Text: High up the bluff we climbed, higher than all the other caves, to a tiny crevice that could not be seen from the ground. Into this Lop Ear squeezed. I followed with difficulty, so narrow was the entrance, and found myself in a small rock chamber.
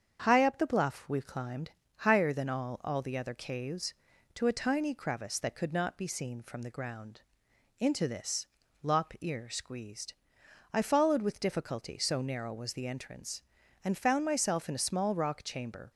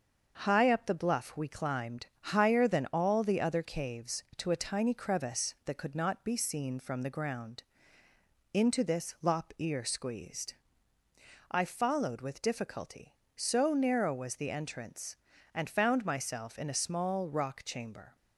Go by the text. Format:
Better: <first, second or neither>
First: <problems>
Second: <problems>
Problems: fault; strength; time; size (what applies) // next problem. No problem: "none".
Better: second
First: starts louder than the rest; strong; until 1.3 s; 7.5 dB // says "all" twice; at 2.8 s // pauses between "this" and "Lop"; at 8.4 s; 0.40 s long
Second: starts louder than the rest; until 1.4 s; 6.5 dB